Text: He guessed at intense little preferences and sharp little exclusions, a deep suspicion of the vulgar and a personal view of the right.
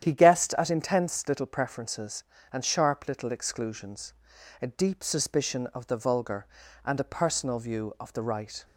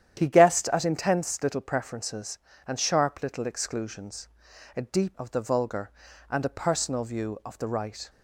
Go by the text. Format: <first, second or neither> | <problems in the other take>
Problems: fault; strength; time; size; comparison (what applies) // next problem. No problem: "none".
first | starts louder than the rest; strong; until 1.2 s; 10 dB; strong in the first // skips "suspicion"; at 5.1 s